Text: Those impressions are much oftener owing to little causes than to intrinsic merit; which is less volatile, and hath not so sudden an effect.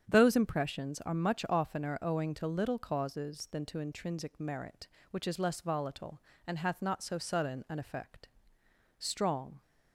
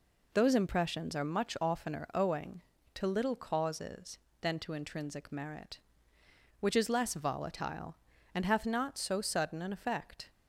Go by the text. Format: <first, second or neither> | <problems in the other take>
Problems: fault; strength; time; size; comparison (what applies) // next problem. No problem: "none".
second | starts louder than the rest; strong; until 1.0 s; 8 dB // goes on to say "Strong"; noticeable; from 8.9 s on; 0.62 s long